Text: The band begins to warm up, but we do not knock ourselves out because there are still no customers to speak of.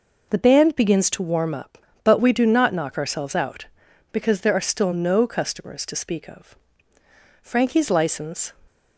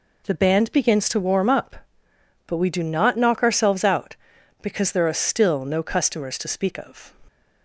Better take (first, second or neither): second